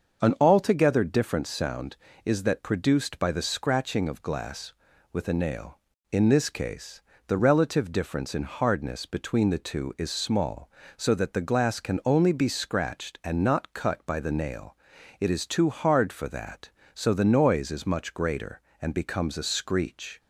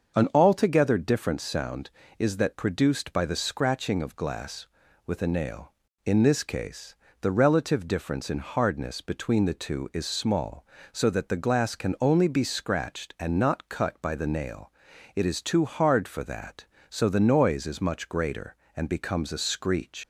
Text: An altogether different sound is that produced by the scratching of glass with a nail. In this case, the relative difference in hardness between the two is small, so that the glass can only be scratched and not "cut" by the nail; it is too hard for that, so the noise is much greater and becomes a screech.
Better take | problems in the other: first | starts louder than the rest; until 1.2 s; 6.5 dB; also in the first // leaves "screech" unfinished; at 20.0 s; 110 ms

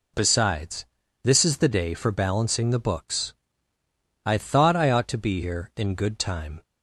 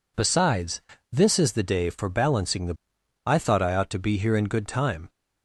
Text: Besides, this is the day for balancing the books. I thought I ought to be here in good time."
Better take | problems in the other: first | skips "books"; at 2.9 s

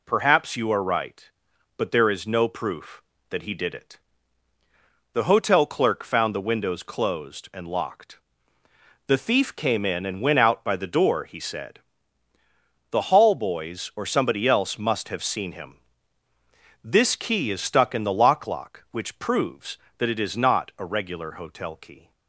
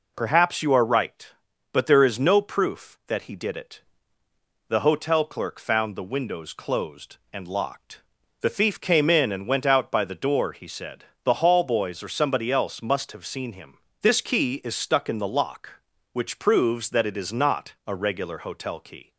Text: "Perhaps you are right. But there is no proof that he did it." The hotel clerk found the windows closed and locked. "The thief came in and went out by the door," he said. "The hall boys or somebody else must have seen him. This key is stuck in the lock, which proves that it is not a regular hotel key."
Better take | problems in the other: second | says "lock" twice; at 18.4 s

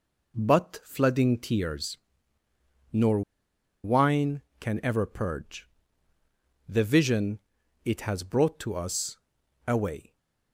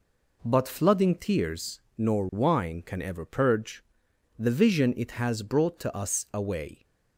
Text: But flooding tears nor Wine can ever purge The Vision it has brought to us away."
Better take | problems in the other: second | pauses between "tears" and "nor"; noticeable; at 1.9 s; 0.94 s long; slight in the second // pauses between "nor" and "Wine"; noticeable; at 3.2 s; 0.62 s long // pauses between "purge" and "The"; at 5.6 s; 1.0 s long; noticeable in the second // pauses between "Vision" and "it"; at 7.3 s; 0.44 s long // pauses between "us" and "away"; noticeable; at 9.1 s; 0.50 s long

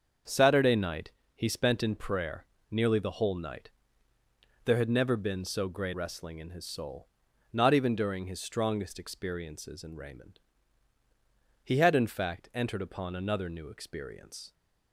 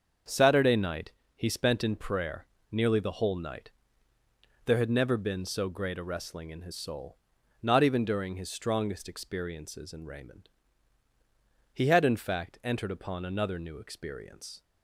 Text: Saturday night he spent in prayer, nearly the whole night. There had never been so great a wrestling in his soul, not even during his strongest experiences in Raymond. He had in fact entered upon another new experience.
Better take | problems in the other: second | starts louder than the rest; until 1.5 s; 6.5 dB; also in the second // pauses between "night" and "he"; slight; at 1.1 s; 0.24 s long; slight in the second // skips "a"; at 5.9 s

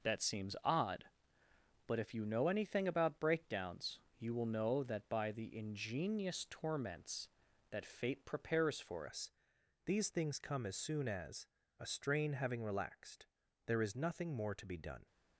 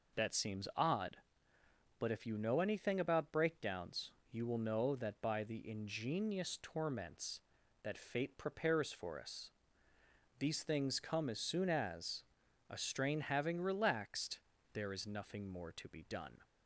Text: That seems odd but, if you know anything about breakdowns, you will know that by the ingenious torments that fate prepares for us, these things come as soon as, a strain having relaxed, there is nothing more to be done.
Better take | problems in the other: second | changes voice at "us"; from 9.0 s on; 6.0 s long

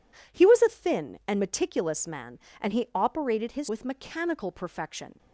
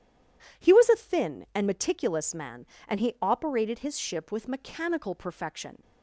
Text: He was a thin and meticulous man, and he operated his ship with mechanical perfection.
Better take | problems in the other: second | skips "ship"; at 3.6 s

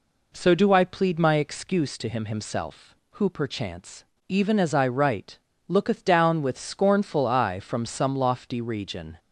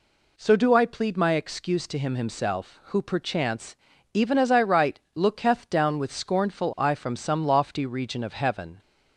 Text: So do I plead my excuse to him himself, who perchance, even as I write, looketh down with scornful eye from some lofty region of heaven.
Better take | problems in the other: second | stops before "of heaven"; at 9.1 s

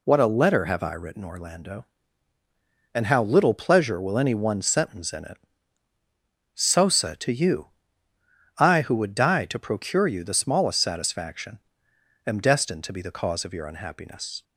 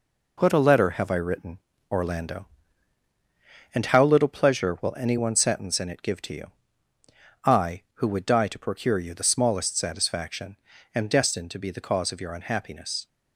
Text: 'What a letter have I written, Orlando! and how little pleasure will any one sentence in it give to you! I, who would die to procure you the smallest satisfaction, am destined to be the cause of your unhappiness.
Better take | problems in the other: second | says "sosa" for "give"; at 6.5 s

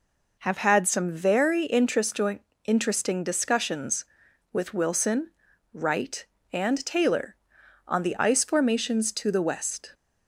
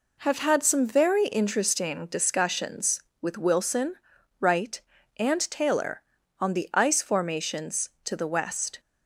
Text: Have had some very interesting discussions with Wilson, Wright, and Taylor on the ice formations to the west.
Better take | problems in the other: second | says "interesting" twice; at 2.6 s

